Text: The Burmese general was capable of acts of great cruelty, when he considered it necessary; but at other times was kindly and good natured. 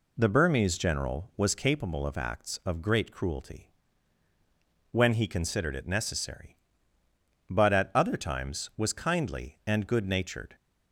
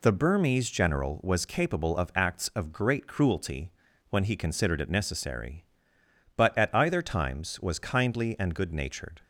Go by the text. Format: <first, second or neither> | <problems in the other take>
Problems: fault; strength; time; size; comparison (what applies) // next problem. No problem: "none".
first | says "either" for "other"; at 6.7 s